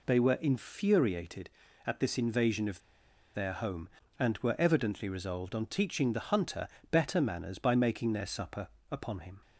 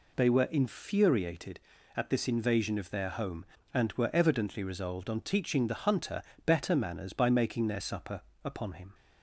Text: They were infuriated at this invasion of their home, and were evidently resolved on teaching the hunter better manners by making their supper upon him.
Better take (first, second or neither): second